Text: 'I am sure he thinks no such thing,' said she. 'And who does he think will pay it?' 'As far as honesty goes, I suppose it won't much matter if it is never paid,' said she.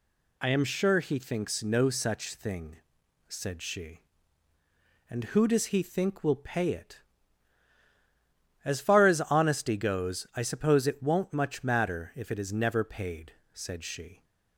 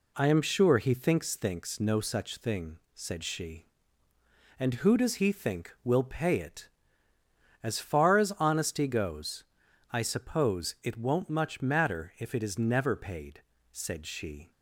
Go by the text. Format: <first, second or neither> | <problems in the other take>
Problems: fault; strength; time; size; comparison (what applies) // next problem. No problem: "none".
first | says "thinks" twice; at 1.3 s